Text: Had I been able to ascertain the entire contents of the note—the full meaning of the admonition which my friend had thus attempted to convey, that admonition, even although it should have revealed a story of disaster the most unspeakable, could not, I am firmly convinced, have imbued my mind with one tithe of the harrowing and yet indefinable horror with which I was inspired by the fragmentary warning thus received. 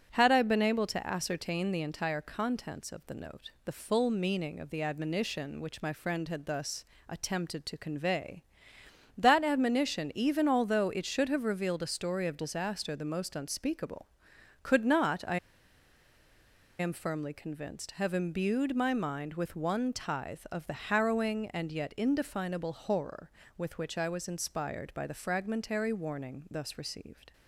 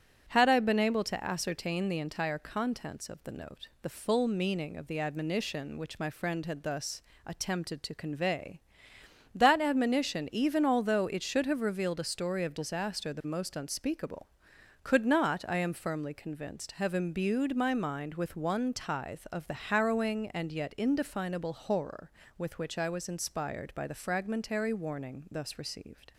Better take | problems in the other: second | starts louder than the rest; strong; until 1.1 s; 8 dB; strong in the second // pauses between "thus" and "attempted"; slight; at 6.8 s; 0.24 s long; slight in the second // pauses between "I" and "am"; strong; at 15.3 s; 1.4 s long

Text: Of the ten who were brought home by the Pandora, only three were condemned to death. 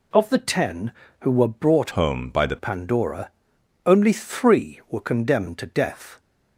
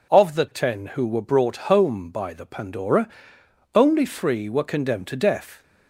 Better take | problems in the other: second | changes voice from "home" to "the"; from 1.9 to 2.5 s; 0.6 s long

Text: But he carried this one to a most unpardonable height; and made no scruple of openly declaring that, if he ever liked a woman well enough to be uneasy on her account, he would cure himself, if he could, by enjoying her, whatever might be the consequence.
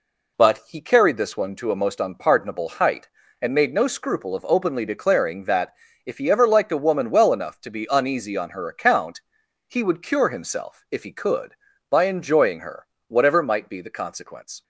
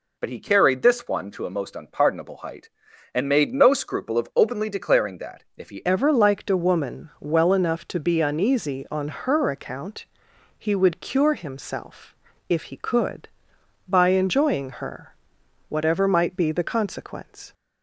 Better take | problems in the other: first | changes voice at "ever"; from 5.8 s on; 11.7 s long

